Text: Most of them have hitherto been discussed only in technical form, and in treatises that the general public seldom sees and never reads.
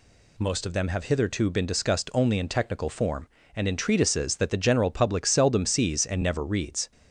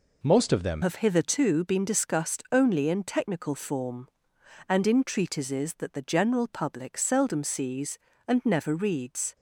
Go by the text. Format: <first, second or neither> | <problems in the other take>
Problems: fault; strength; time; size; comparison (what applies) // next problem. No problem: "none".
first | changes voice at "have"; from 0.8 s on; 8.5 s long